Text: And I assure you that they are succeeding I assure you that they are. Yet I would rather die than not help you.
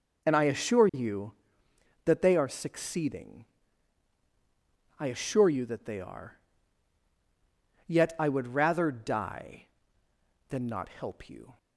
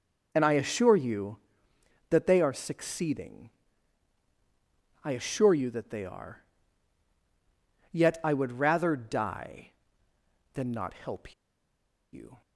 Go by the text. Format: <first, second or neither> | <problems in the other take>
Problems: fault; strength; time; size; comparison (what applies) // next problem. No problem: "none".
first | pauses between "succeeding" and "I"; strong; at 3.4 s; 1.5 s long; strong in the first // pauses between "help" and "you"; noticeable; at 11.3 s; 0.78 s long